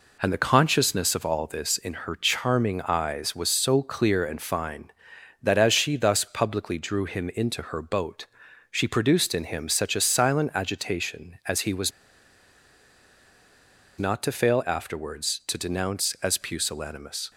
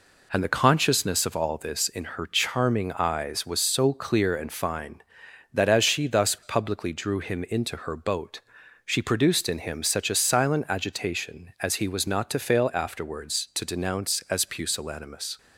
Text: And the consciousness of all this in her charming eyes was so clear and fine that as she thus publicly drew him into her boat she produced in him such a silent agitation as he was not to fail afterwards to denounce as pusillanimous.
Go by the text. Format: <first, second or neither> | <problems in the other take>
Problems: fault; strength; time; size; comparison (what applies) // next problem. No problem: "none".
second | pauses between "boat" and "she"; noticeable; at 8.2 s; 0.46 s long; noticeable in the second // pauses between "was" and "not"; strong; at 11.9 s; 2.0 s long